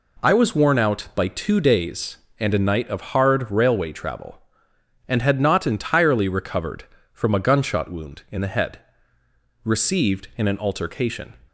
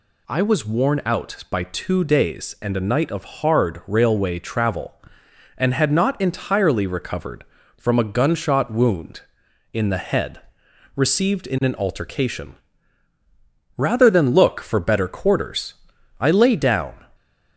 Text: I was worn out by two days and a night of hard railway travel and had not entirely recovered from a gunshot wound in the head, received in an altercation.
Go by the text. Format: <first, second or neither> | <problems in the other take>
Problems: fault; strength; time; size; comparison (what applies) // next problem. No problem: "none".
first | goes on to say "Rather than look for better quarters I lay down"; strong; from 13.7 s on; 3.2 s long